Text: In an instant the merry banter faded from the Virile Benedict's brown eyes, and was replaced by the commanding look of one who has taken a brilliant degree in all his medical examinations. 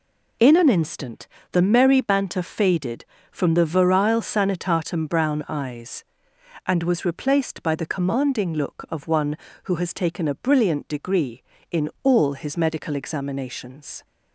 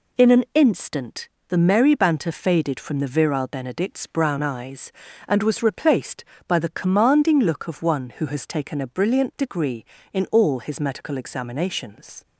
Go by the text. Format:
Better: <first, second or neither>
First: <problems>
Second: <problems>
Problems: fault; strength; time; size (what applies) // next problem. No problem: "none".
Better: second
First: pauses between "instant" and "the"; slight; at 1.2 s; 0.24 s long // says "Sanitatum" for "Benedict's"; at 4.2 s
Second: pauses between "instant" and "the"; slight; at 1.2 s; 0.20 s long